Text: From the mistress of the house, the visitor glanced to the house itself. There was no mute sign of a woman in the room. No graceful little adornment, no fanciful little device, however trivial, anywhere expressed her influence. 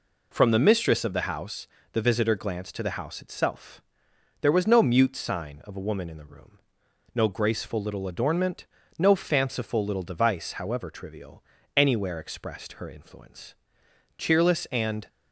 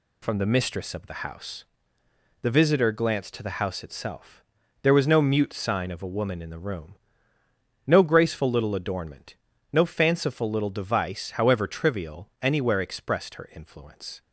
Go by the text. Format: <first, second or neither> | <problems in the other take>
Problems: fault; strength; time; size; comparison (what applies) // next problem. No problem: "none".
second | goes on to say "Cheerless and"; noticeable; from 14.1 s on; 0.92 s long